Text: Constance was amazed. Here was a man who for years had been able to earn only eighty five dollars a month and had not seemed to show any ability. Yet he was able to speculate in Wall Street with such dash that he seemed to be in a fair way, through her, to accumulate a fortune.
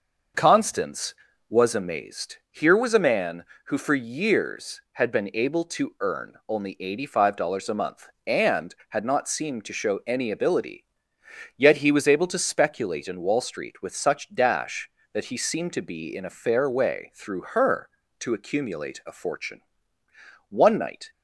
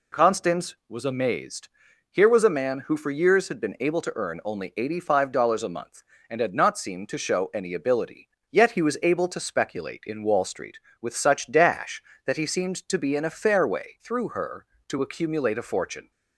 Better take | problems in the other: second | starts louder than the rest; noticeable; until 1.7 s; 6 dB // pauses between "earn" and "only"; slight; at 6.3 s; 0.16 s long // goes on to say "One night"; from 20.4 s on; 0.60 s long

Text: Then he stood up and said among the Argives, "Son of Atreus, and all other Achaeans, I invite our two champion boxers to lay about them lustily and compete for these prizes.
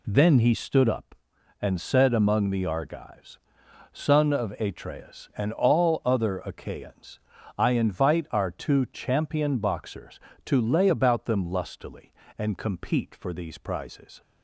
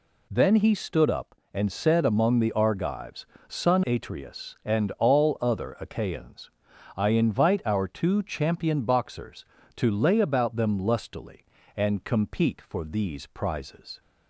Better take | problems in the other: first | skips "of"; at 3.8 s

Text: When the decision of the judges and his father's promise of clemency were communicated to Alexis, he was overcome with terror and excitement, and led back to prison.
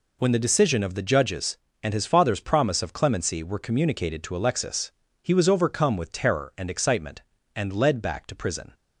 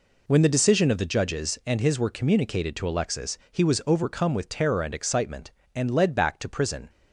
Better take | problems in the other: first | skips "father's promise of clemency"; at 2.0 s

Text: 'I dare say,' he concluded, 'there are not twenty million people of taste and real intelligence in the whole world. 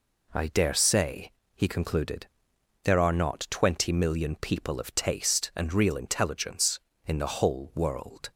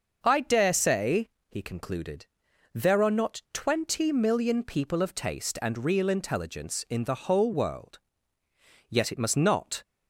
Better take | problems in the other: first | starts louder than the rest; noticeable; until 1.2 s; 6 dB // goes on to say "Yet it must not"; noticeable; from 8.9 s on; 0.92 s long

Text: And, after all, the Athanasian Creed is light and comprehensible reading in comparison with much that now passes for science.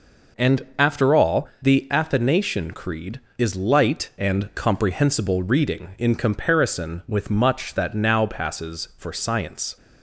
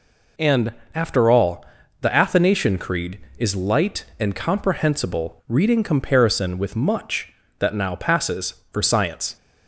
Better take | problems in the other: first | skips "in"; at 5.8 s

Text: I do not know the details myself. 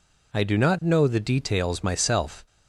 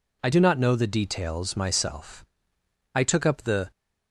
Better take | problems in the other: first | goes on to say "I took up the"; noticeable; from 2.9 s on; 0.78 s long

